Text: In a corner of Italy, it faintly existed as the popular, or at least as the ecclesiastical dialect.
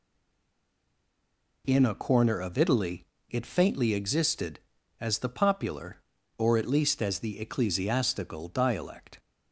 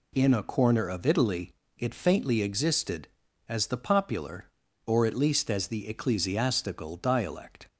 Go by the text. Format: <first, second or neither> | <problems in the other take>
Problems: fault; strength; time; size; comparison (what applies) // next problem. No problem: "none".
second | stays silent before the first word; noticeable; until 1.6 s; 1.6 s long